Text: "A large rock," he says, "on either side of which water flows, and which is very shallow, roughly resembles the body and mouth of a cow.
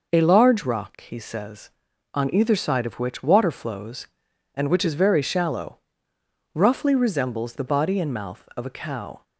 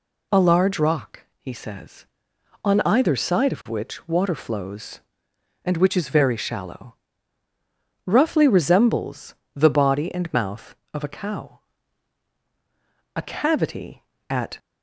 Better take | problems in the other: first | pauses between "resembles" and "the"; slight; at 9.3 s; 0.20 s long // goes on to say "A cavity at"; from 13.1 s on; 1.4 s long

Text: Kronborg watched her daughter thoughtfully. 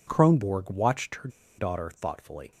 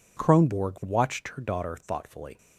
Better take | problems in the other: second | pauses between "her" and "daughter"; slight; at 1.2 s; 0.29 s long

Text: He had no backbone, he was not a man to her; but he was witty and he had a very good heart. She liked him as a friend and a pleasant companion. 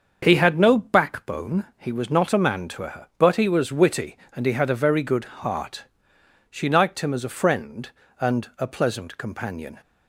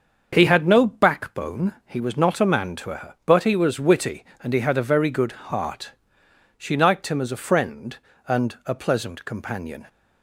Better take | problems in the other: neither | starts louder than the rest; the same in both // pauses between "good" and "heart"; slight; the same in both

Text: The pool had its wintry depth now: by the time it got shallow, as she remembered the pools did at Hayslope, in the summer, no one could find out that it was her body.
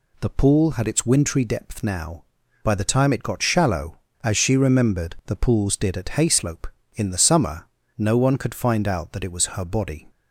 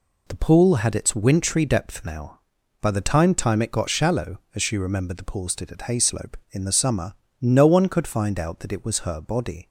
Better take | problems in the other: first | says "time" twice; at 3.3 s

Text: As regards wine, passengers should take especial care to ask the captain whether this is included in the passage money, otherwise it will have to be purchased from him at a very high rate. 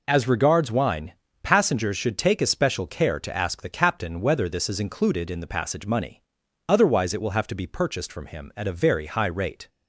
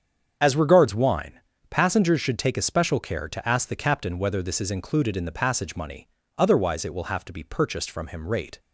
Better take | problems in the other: first | starts louder than the rest; strong; until 1.4 s; 7.5 dB // skips "at a very high"; at 8.2 s

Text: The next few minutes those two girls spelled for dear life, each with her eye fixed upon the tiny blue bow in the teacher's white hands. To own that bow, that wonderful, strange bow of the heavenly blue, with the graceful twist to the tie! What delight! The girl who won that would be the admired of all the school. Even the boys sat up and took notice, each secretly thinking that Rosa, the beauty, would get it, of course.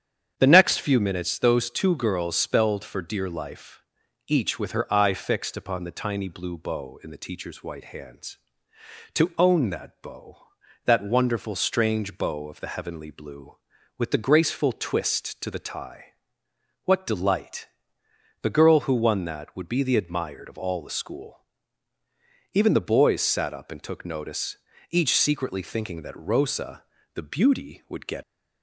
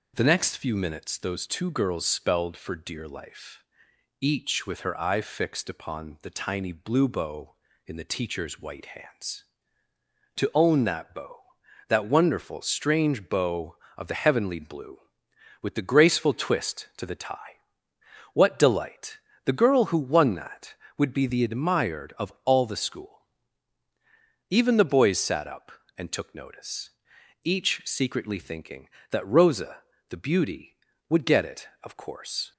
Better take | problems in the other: second | starts louder than the rest; strong; until 1.3 s; 8.5 dB // stops before "it of course"; at 28.2 s

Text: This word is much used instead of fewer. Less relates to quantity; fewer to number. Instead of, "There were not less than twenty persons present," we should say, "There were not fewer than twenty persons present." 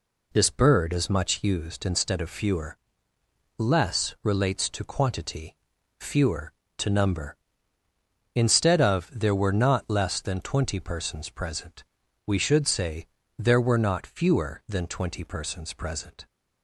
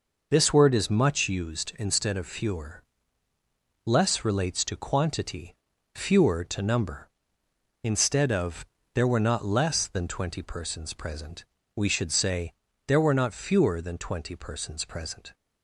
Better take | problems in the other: second | says "bird" for "word"; at 0.4 s

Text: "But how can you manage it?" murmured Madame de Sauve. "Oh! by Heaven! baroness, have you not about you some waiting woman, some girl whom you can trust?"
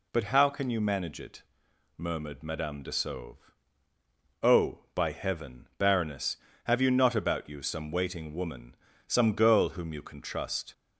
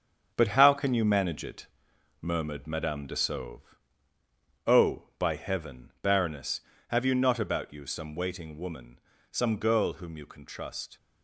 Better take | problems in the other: first | gets quieter; throughout; 7 dB

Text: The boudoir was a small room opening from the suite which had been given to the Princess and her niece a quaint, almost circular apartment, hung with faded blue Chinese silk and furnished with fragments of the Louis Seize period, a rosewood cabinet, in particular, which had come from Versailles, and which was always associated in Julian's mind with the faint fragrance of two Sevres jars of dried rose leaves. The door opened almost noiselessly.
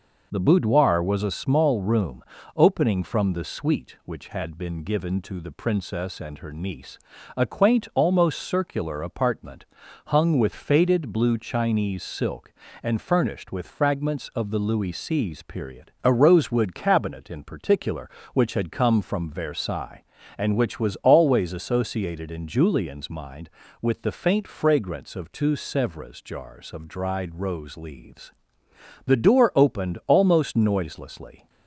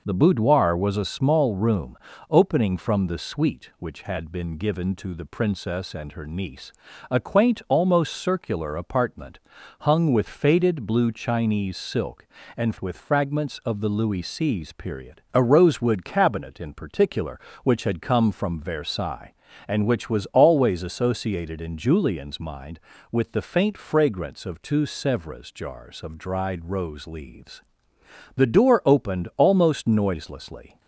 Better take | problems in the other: first | pauses between "room" and "opening"; slight; at 1.9 s; 0.34 s long; slight in the first // pauses between "niece" and "a"; slight; at 6.7 s; 0.36 s long; slight in the first // skips "furnished"; at 12.7 s

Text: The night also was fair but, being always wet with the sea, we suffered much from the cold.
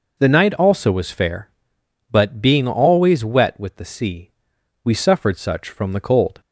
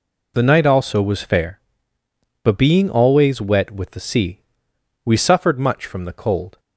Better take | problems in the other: second | says "such" for "much"; at 5.3 s

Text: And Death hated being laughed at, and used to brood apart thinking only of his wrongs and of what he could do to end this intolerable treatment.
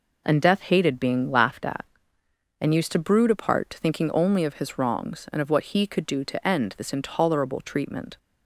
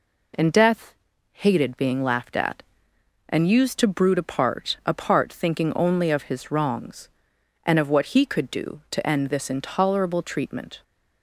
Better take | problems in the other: first | pauses between "Death" and "hated"; at 0.9 s; 0.38 s long // says "apart" twice; at 4.8 s

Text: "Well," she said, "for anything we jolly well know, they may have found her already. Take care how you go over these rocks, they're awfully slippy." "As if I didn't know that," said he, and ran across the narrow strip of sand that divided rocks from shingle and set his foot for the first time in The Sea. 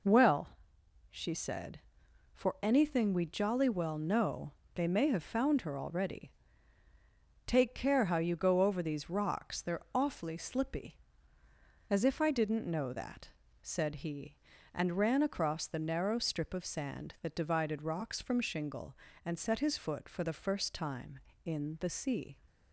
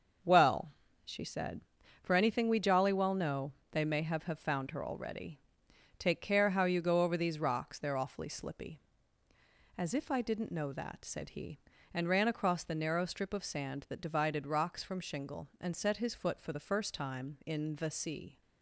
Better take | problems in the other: first | starts louder than the rest; until 1.5 s; 6.5 dB // says "have" twice; at 4.2 s

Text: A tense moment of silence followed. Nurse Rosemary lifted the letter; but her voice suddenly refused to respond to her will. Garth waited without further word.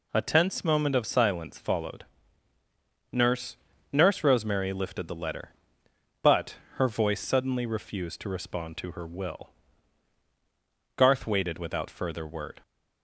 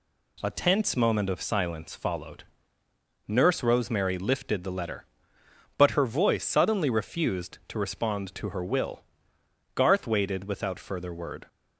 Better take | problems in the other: second | says "Nurse" twice; at 3.9 s // pauses between "but" and "her"; slight; at 6.5 s; 0.22 s long

